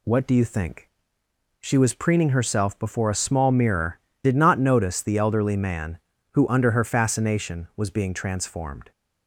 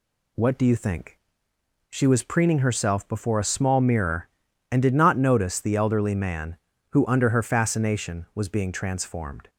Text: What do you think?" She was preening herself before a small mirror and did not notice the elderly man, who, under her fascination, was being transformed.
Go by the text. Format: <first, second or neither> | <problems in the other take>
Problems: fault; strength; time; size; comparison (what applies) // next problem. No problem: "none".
second | skips "and"; at 4.1 s